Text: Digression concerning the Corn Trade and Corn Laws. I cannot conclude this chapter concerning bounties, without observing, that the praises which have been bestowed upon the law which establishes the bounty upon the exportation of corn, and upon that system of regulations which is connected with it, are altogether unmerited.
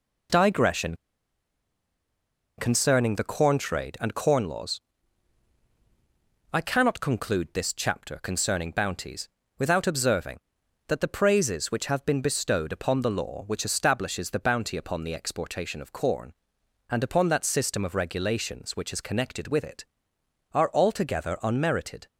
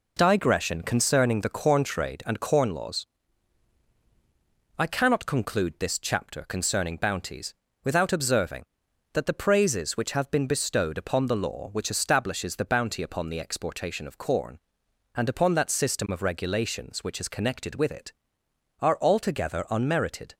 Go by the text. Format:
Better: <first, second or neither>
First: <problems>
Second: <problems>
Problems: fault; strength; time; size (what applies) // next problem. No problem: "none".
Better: second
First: pauses between "Digression" and "concerning"; strong; at 0.9 s; 1.6 s long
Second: none